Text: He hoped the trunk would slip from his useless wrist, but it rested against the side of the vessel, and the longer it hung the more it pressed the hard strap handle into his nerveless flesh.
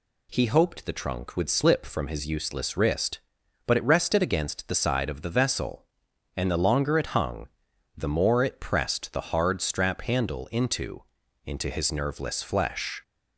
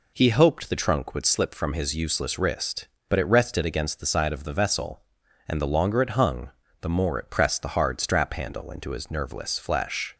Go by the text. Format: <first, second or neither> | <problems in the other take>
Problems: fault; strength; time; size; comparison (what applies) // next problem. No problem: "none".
second | pauses between "hung" and "the"; noticeable; at 7.4 s; 0.48 s long; slight in the second // says "into" twice; at 11.4 s